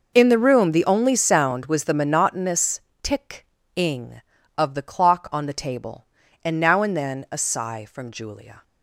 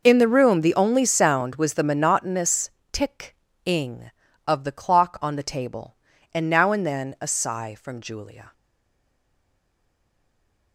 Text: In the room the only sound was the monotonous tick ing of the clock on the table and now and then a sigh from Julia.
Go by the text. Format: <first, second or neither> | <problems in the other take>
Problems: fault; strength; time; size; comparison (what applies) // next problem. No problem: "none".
first | pauses between "monotonous" and "tick"; slight; at 2.7 s; 0.20 s long; slight in the first // pauses between "tick" and "ing"; slight; at 3.3 s; 0.28 s long; slight in the first // stays silent after the last word; from 8.5 s on; 2.2 s long